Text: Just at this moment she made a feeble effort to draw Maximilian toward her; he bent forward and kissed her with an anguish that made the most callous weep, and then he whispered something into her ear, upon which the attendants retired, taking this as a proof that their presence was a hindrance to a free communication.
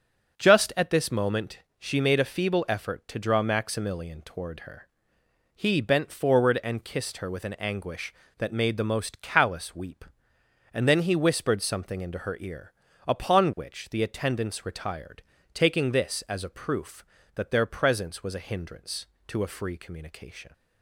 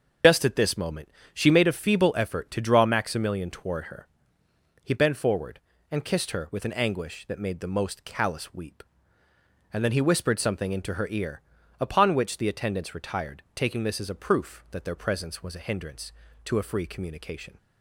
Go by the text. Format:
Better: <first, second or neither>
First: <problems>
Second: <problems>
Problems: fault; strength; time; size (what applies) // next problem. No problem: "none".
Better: first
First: starts louder than the rest; until 1.3 s; 6 dB // pauses between "moment" and "she"; slight; at 1.5 s; 0.20 s long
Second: loses the start of "Just"; at 0.2 s; 75 ms // starts louder than the rest; until 1.5 s; 6.5 dB // pauses between "moment" and "she"; slight; at 1.0 s; 0.25 s long